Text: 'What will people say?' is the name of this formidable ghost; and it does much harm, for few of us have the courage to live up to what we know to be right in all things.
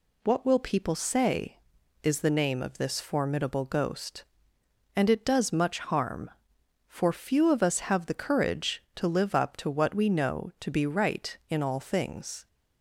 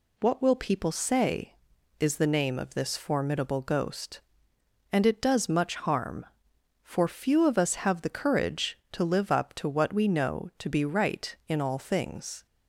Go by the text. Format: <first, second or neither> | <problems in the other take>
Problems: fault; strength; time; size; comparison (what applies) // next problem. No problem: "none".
neither | none